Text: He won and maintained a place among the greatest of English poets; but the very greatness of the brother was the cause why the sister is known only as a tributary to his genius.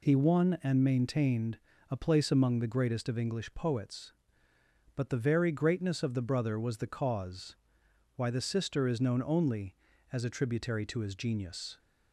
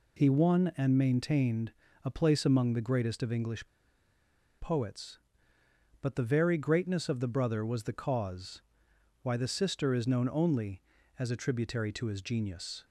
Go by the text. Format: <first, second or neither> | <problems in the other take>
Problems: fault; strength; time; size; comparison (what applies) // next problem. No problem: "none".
first | pauses between "maintained" and "a"; slight; at 1.7 s; 0.32 s long; slight in the first // pauses between "English" and "poets"; noticeable; at 3.6 s; 0.91 s long // pauses between "cause" and "why"; noticeable; at 8.6 s; 0.62 s long; noticeable in the first